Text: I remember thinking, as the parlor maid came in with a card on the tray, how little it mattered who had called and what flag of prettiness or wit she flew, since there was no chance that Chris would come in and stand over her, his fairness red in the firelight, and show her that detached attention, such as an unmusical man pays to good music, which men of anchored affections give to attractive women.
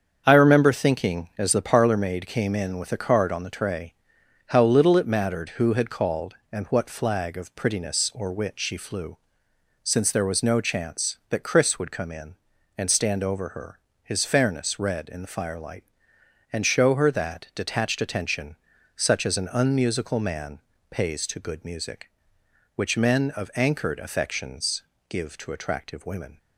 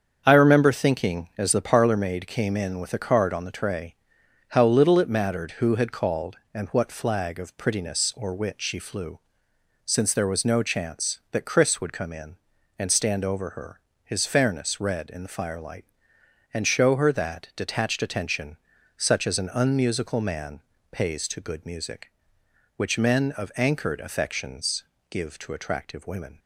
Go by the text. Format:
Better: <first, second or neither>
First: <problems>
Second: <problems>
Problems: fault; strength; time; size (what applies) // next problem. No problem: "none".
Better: neither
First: starts louder than the rest; until 1.2 s; 7 dB // pauses between "man" and "pays"; slight; at 20.5 s; 0.32 s long // pauses between "affections" and "give"; slight; at 24.8 s; 0.26 s long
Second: starts louder than the rest; until 1.2 s; 7 dB // pauses between "man" and "pays"; slight; at 20.6 s; 0.32 s long // pauses between "affections" and "give"; slight; at 24.8 s; 0.26 s long